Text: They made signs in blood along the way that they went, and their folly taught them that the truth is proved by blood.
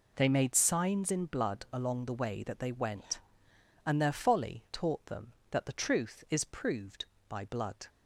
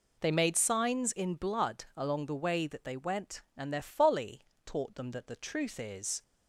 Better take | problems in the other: first | pauses between "folly" and "taught"; slight; at 4.3 s; 0.26 s long // stops before "proved by blood"; at 6.2 s

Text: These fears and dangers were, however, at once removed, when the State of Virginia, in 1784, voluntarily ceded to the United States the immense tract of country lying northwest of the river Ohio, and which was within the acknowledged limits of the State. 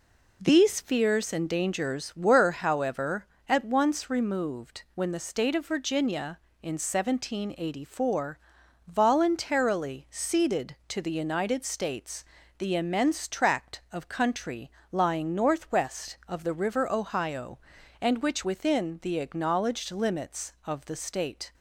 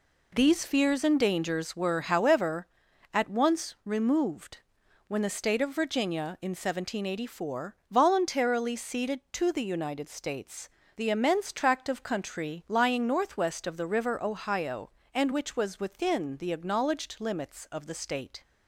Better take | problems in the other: second | pauses between "States" and "the"; slight; at 12.2 s; 0.32 s long; slight in the second // pauses between "country" and "lying"; slight; at 14.7 s; 0.20 s long // skips "was"; at 18.4 s

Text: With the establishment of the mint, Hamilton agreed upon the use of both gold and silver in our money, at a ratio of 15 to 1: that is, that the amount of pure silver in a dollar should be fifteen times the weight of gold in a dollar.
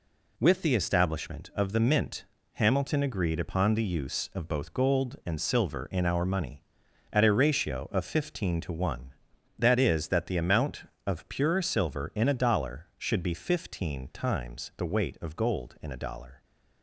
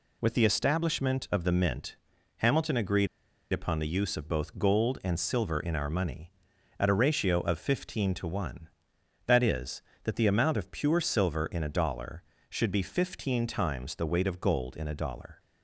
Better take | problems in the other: first | pauses between "agreed" and "upon"; noticeable; at 3.0 s; 0.46 s long

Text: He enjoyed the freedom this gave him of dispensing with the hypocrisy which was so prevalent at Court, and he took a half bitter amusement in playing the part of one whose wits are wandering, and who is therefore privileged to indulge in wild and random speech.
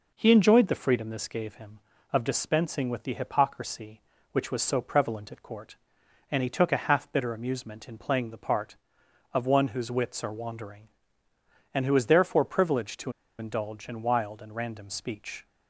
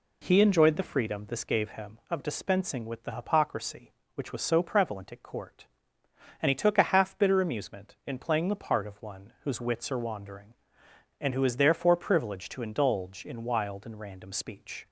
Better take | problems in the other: second | pauses between "to" and "indulge"; slight; at 13.1 s; 0.28 s long

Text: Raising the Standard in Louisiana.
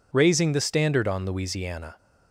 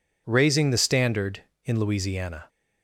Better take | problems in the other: second | says "on" for "in"; at 1.0 s

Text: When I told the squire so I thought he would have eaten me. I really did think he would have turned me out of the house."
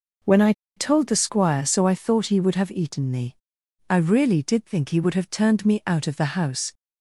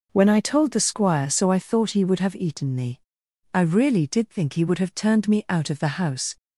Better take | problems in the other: second | pauses between "I" and "told"; slight; at 0.5 s; 0.24 s long

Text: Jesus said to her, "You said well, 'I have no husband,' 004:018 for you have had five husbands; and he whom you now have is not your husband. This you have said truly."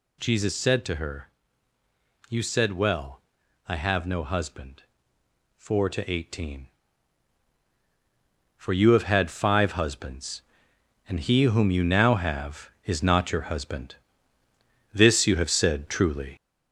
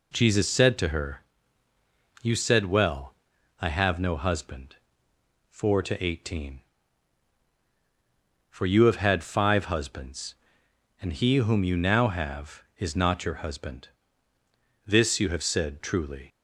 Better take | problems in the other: second | gets louder; noticeable; throughout; 4.5 dB

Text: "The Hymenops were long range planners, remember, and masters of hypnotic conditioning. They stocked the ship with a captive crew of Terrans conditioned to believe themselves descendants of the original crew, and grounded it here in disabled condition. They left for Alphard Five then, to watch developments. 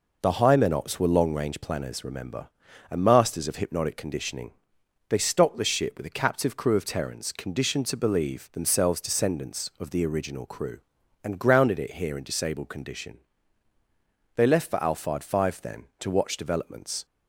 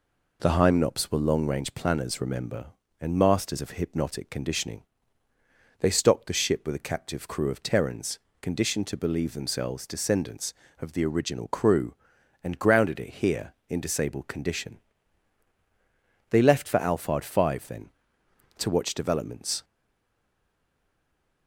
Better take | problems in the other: first | pauses between "Terrans" and "conditioned"; slight; at 8.1 s; 0.24 s long // stays silent after the last word; noticeable; from 19.6 s on; 1.8 s long

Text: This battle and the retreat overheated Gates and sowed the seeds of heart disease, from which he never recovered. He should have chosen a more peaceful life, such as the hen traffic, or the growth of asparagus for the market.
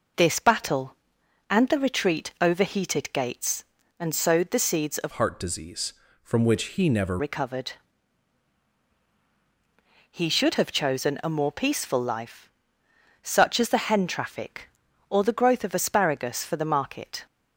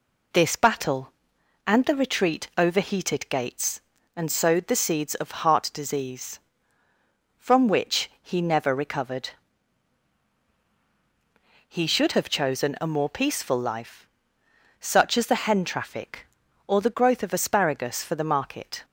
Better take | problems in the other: second | changes voice from "heart" to "never"; from 5.1 to 7.1 s; 2.0 s long

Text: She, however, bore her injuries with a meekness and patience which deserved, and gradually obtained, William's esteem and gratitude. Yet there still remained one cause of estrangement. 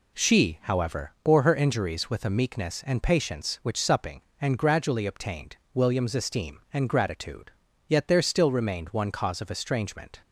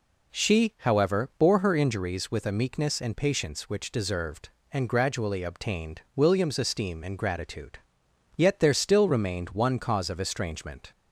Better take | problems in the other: second | says "supping" for "deserved"; at 3.8 s

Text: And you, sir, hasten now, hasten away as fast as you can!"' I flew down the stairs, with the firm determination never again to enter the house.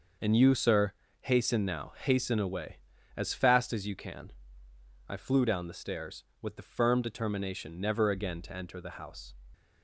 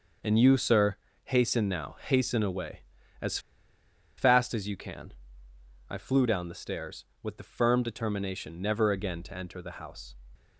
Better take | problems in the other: first | pauses between "as" and "fast"; noticeable; at 3.3 s; 0.79 s long

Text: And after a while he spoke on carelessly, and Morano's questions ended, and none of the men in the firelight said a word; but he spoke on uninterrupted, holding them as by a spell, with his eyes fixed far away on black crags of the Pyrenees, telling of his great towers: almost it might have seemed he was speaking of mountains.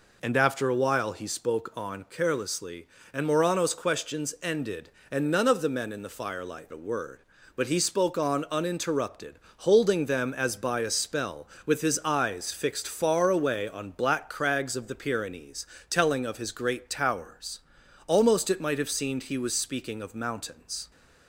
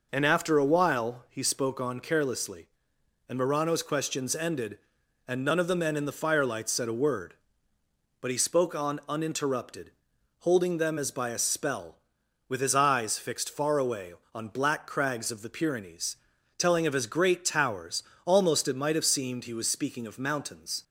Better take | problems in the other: second | skips "said"; at 6.7 s

